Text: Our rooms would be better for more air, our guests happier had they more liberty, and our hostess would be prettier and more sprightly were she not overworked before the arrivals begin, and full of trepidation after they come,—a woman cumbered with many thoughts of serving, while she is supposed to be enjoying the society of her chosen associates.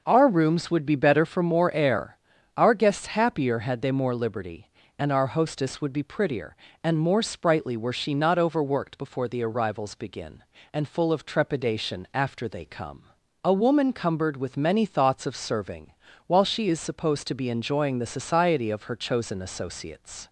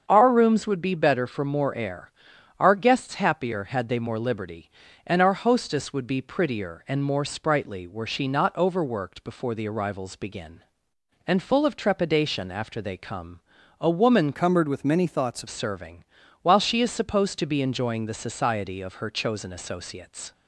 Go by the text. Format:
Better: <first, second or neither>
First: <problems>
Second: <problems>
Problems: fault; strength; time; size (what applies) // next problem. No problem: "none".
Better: first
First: none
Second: starts louder than the rest; strong; until 1.0 s; 7 dB // changes voice from "cumbered" to "of"; from 14.3 to 15.4 s; 1.1 s long